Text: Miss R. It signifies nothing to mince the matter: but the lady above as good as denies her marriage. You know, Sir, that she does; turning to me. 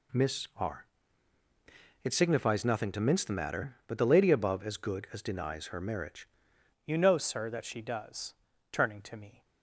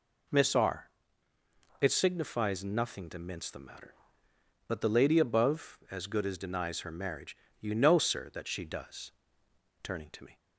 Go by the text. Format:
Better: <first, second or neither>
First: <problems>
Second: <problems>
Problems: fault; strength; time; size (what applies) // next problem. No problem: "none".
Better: second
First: changes voice at "You"; from 6.8 s on; 2.6 s long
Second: none